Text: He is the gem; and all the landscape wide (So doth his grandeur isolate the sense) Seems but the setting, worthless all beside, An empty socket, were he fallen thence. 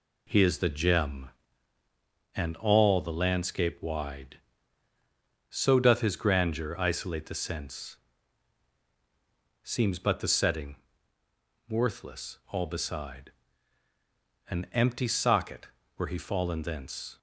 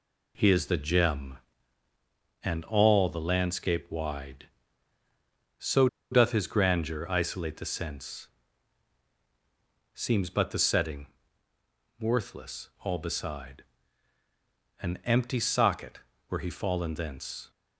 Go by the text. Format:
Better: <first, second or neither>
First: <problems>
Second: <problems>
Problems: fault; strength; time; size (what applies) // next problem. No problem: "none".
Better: first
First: none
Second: pauses between "So" and "doth"; slight; at 5.8 s; 0.23 s long